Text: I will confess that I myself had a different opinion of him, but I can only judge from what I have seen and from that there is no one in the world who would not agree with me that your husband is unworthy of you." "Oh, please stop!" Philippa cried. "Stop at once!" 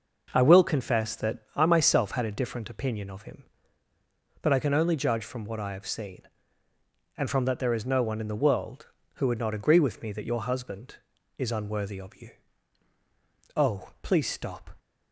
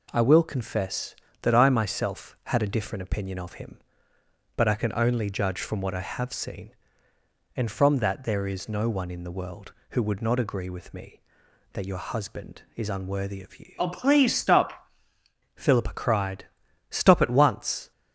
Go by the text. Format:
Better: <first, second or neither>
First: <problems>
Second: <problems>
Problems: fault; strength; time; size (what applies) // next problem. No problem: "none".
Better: second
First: pauses between "that" and "I"; slight; at 1.3 s; 0.16 s long // stops before "Philippa cried Stop at once"; at 14.7 s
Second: none